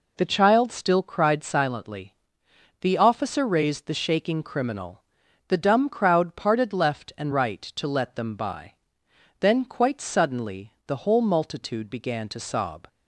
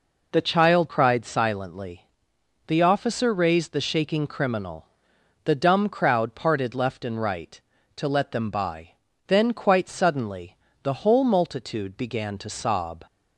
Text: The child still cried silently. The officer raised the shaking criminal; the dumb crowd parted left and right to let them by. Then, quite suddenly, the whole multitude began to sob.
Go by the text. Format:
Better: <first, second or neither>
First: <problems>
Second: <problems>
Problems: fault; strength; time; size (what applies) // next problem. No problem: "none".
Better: first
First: none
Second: skips "still"; at 0.8 s